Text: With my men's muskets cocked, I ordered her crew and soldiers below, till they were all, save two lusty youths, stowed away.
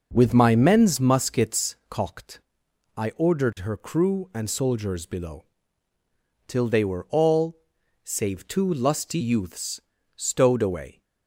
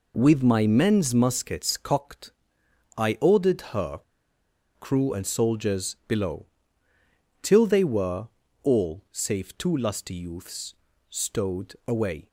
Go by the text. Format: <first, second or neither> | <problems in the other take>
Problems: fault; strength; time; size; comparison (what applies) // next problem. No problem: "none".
first | pauses between "her" and "crew"; noticeable; at 3.9 s; 0.78 s long // pauses between "were" and "all"; slight; at 8.2 s; 0.34 s long